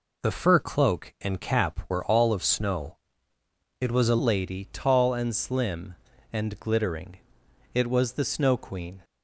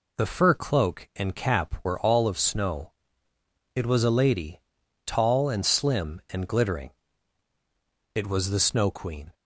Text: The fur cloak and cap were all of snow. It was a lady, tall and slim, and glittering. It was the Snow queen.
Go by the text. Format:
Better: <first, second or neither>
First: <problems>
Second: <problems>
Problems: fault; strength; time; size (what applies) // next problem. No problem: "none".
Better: second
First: changes voice at "lady"; from 4.1 s on; 4.9 s long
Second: none